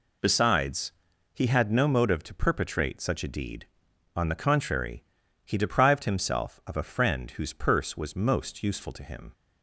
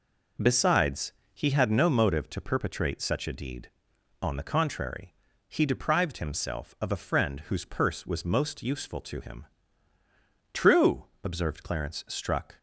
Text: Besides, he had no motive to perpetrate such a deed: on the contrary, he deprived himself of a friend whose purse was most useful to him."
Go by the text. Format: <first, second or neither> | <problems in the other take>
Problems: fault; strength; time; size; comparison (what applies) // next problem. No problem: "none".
first | goes on to say "True observed Clarence struck"; strong; from 10.5 s on; 2.0 s long